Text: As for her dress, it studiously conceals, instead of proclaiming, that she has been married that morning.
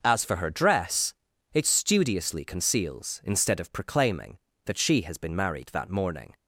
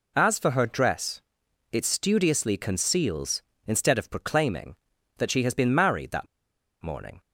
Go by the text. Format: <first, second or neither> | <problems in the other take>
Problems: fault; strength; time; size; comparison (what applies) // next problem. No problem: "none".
first | pauses between "that" and "morning"; noticeable; at 6.2 s; 0.55 s long